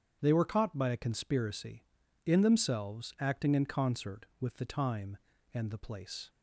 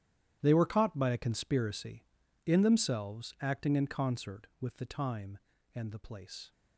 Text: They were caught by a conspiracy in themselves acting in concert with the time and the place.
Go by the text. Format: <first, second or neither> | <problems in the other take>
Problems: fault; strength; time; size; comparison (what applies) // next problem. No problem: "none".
first | gets quieter; strong; throughout; 16 dB // starts louder than the rest; strong; until 1.4 s; 11 dB; strong in the first